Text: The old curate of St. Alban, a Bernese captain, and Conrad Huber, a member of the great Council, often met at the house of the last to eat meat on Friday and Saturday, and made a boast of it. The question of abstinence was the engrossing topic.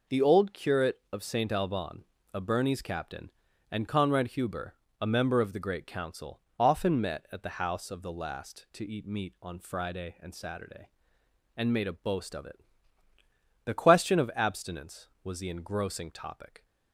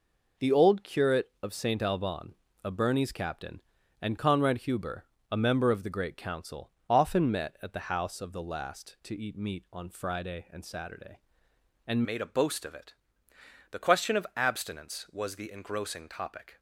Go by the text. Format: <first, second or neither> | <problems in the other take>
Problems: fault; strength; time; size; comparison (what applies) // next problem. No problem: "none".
first | changes voice at "made"; from 12.0 s on; 4.5 s long